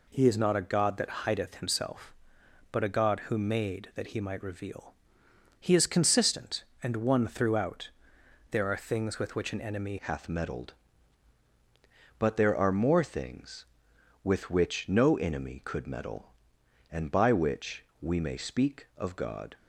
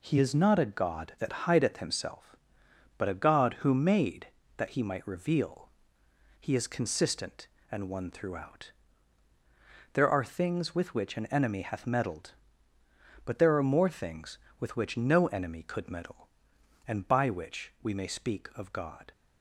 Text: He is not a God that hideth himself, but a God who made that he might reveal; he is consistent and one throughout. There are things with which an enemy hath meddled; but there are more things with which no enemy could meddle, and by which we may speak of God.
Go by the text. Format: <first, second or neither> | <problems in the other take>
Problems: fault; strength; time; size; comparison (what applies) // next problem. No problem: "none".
second | changes voice at "hath"; from 9.9 s on; 9.6 s long // pauses between "which" and "we"; slight; at 17.8 s; 0.16 s long